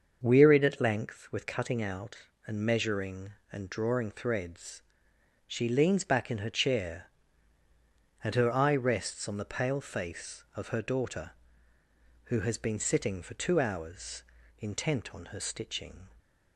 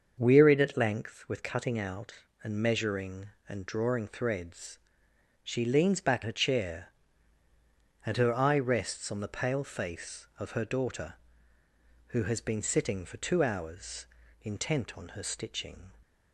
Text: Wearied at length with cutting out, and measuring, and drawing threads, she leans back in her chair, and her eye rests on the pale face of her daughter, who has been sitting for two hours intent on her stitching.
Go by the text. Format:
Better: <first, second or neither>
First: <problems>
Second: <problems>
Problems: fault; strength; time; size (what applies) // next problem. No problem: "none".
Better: first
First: starts louder than the rest; until 1.2 s; 6.5 dB // pauses between "hours" and "intent"; at 14.2 s; 0.38 s long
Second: starts louder than the rest; until 1.1 s; 6.5 dB // skips "in"; at 6.2 s // pauses between "hours" and "intent"; at 14.0 s; 0.38 s long